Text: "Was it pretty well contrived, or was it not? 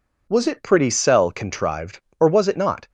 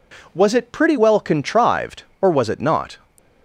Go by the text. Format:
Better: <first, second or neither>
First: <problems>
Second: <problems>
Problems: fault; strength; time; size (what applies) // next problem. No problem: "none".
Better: second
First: says "cell" for "well"; at 0.8 s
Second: none